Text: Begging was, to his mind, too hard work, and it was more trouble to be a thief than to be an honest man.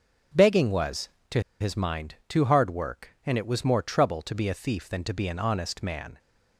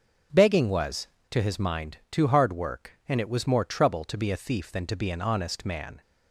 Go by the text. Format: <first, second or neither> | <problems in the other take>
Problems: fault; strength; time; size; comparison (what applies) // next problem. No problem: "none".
second | pauses between "to" and "his"; slight; at 1.4 s; 0.18 s long